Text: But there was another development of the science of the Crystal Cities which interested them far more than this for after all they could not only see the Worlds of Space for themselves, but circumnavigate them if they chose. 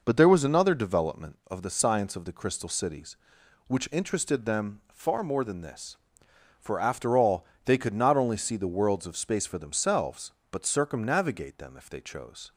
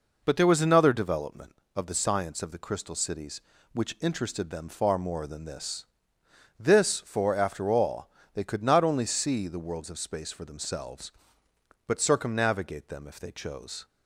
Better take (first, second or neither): first